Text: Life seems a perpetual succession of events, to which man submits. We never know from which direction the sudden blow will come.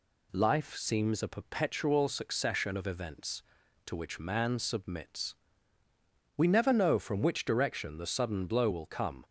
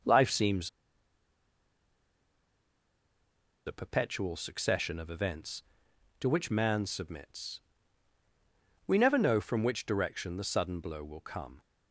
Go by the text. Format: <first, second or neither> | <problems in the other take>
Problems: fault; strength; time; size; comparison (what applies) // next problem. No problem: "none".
first | pauses between "seems" and "a"; strong; at 0.6 s; 2.9 s long